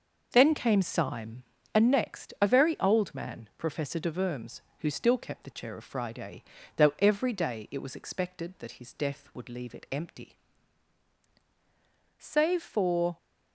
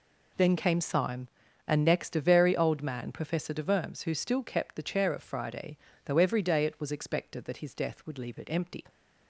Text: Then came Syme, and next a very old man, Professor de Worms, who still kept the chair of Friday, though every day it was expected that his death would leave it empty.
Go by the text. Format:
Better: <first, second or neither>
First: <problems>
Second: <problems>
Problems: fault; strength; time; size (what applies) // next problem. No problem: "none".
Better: second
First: goes on to say "Save for"; noticeable; from 12.1 s on; 0.98 s long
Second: none